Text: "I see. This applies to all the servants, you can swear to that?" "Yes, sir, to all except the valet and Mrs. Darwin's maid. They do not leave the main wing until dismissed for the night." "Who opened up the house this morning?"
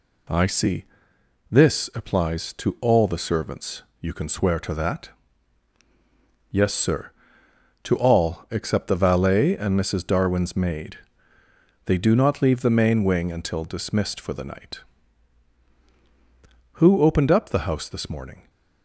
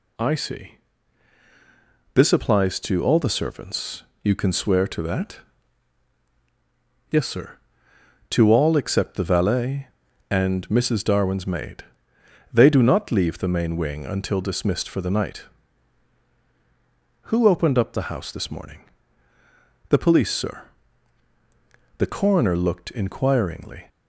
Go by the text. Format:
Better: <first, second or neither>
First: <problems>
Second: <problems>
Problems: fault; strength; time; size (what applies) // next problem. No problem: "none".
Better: first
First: none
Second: goes on to say "The police sir The coroner looked inquiringly"; strong; from 19.9 s on; 3.9 s long